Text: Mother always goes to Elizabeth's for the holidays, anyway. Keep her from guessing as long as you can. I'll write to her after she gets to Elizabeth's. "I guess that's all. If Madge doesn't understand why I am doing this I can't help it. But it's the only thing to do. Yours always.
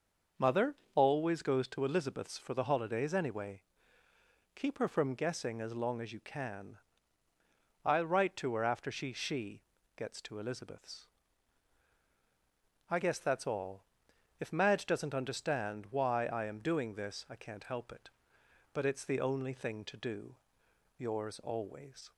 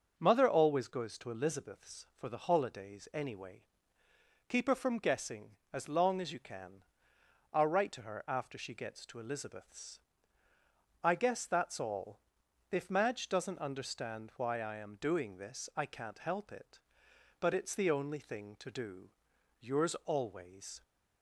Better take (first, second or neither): second